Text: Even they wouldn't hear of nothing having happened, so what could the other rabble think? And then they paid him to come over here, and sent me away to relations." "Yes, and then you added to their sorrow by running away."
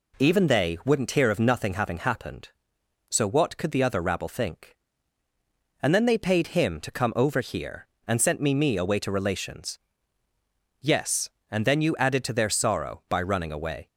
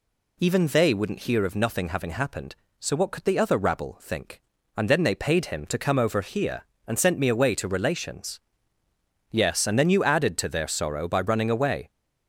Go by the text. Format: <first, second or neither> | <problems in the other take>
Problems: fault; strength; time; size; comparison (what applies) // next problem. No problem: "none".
second | says "me" twice; at 8.5 s